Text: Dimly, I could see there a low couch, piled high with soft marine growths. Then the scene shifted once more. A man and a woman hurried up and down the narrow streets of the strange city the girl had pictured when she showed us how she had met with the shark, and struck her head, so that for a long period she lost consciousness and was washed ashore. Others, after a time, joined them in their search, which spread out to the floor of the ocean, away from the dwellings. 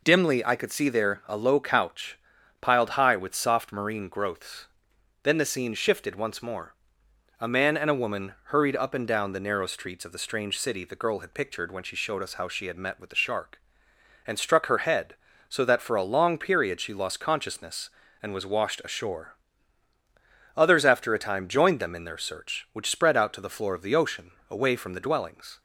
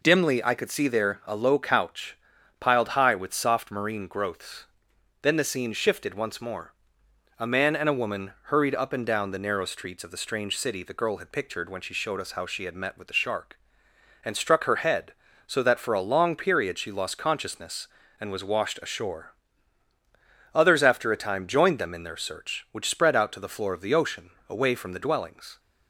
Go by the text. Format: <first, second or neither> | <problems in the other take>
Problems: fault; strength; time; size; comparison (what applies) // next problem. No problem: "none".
neither | none